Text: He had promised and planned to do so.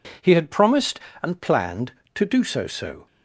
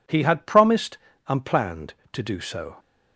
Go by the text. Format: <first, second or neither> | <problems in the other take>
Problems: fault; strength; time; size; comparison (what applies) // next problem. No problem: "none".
second | says "so" twice; at 2.6 s